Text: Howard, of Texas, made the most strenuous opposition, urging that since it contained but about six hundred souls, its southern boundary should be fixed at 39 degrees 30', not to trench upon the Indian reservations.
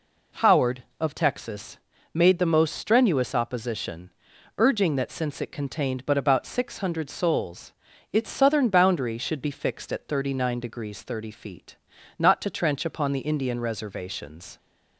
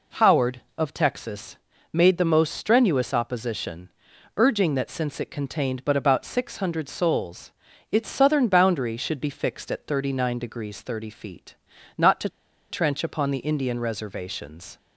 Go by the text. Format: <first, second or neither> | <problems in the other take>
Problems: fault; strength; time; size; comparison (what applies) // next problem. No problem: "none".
first | pauses between "to" and "trench"; at 12.2 s; 0.42 s long